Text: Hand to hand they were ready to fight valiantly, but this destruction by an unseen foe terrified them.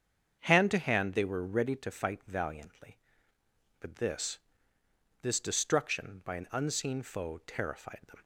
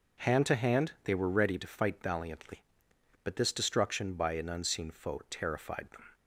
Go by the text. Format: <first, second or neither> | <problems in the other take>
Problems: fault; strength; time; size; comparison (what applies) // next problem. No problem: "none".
second | starts louder than the rest; strong; until 1.4 s; 7.5 dB // says "this" twice; at 5.2 s